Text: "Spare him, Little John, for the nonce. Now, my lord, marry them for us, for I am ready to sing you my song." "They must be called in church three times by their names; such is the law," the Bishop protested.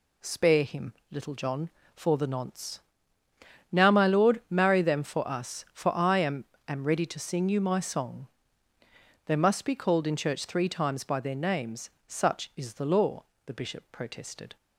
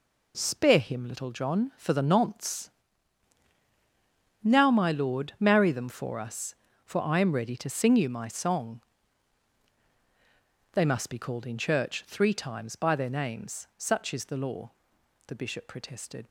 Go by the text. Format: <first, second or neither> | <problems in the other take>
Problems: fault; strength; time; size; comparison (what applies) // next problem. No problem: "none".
second | says "am" twice; at 6.6 s